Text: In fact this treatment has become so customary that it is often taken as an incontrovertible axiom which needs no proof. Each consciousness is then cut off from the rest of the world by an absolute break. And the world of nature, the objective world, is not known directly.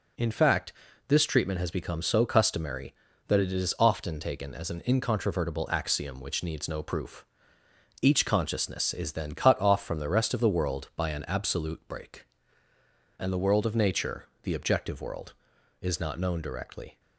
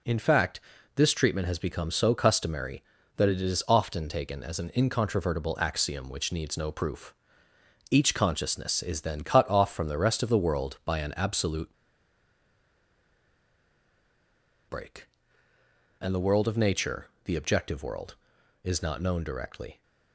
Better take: first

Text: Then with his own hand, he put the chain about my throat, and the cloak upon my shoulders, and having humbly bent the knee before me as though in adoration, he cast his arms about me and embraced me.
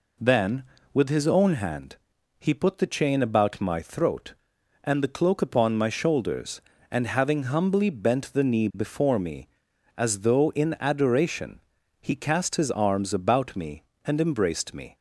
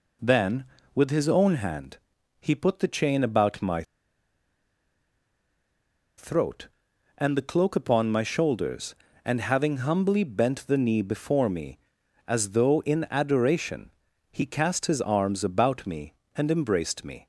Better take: first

